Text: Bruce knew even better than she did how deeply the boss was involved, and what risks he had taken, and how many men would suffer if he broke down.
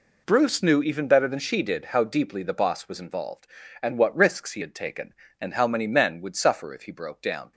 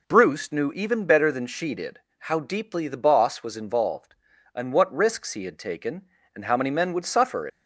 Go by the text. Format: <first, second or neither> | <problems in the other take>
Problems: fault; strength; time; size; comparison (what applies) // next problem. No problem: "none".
first | pauses between "did" and "how"; slight; at 1.9 s; 0.20 s long // stops before "if he broke down"; at 7.4 s